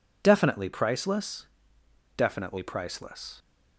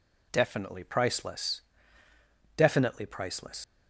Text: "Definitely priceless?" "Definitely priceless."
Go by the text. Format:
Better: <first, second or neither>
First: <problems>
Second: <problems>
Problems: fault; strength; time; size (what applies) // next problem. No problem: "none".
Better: first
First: none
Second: leaves "priceless" unfinished; at 3.6 s; 90 ms